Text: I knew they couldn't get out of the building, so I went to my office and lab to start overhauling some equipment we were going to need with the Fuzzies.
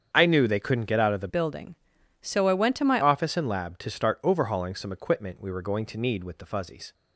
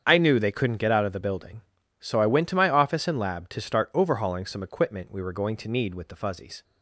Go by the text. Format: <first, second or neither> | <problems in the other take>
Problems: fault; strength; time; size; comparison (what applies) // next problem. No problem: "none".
second | starts louder than the rest; strong; until 1.1 s; 8 dB; strong in the second // changes voice from "building" to "my"; from 1.2 to 3.0 s; 1.8 s long